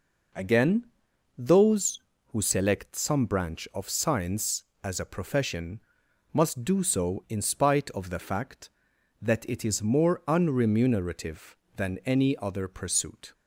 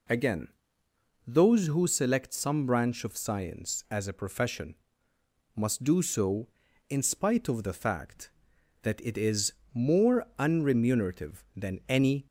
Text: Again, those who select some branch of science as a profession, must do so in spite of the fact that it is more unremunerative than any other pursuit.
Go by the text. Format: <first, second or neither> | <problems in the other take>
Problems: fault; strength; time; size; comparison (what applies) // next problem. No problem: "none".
first | pauses between "is" and "more"; slight; at 9.5 s; 0.20 s long // stops before "other pursuit"; at 12.2 s